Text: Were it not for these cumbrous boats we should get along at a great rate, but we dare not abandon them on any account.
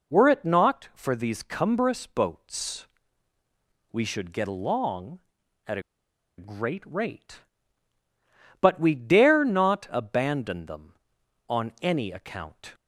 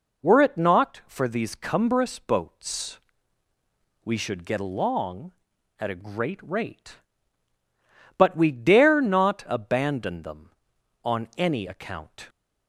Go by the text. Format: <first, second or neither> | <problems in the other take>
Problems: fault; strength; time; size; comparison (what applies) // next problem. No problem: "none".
second | pauses between "boats" and "we"; at 2.8 s; 1.0 s long; also in the second // pauses between "a" and "great"; noticeable; at 5.8 s; 0.56 s long